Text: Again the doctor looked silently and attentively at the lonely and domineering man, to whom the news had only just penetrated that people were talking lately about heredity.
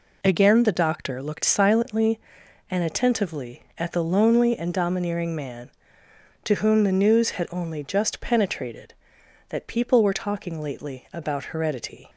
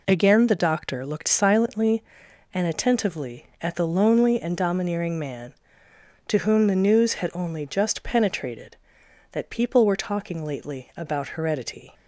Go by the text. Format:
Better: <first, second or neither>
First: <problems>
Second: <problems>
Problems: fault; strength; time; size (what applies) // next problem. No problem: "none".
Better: neither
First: none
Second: none